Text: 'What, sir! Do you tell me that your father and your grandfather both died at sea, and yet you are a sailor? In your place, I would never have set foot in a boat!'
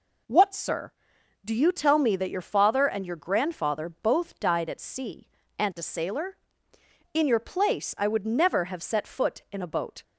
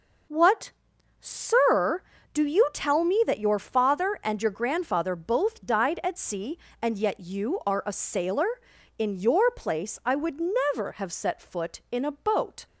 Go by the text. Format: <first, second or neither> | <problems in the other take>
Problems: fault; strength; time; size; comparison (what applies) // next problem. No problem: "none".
second | skips "yet you are"; at 5.7 s